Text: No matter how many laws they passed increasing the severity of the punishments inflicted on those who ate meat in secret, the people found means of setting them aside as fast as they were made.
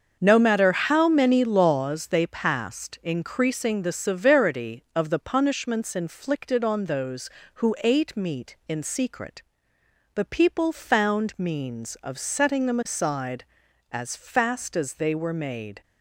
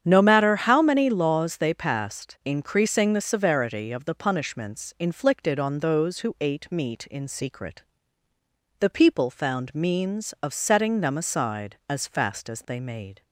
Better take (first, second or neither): first